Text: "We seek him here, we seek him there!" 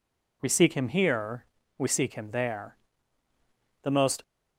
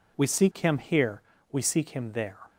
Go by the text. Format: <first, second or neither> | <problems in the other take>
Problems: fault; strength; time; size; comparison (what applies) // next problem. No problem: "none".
second | goes on to say "The most"; slight; from 3.8 s on; 0.40 s long